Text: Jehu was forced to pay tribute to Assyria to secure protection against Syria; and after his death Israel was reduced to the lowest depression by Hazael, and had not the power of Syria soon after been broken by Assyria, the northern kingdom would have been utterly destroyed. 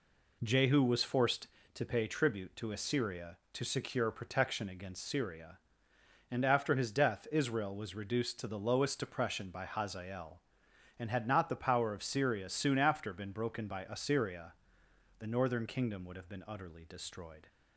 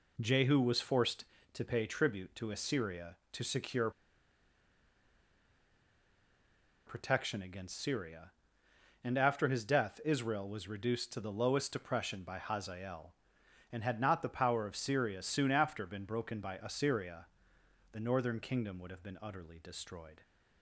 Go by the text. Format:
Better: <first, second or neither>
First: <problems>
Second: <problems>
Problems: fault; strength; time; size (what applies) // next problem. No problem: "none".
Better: first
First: none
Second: pauses between "secure" and "protection"; strong; at 3.8 s; 2.9 s long